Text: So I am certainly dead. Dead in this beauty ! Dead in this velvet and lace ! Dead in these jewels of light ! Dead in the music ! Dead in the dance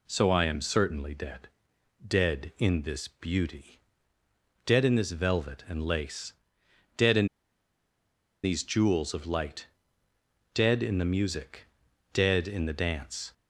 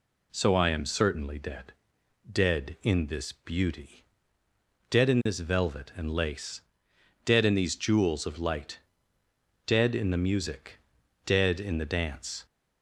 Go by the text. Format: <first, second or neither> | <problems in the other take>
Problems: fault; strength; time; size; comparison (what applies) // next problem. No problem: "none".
second | pauses between "in" and "these"; at 7.2 s; 1.1 s long